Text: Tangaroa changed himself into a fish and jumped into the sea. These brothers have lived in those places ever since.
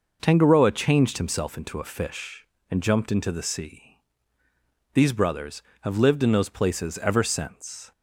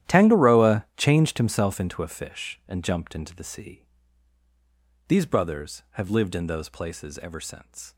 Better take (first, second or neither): first